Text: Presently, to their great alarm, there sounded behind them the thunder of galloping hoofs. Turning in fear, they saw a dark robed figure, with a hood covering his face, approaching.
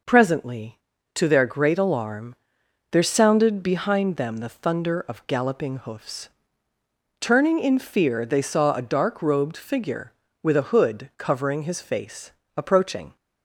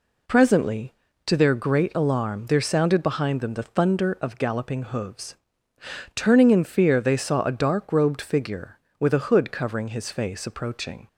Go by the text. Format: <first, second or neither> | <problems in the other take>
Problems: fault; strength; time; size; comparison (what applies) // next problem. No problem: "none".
neither | none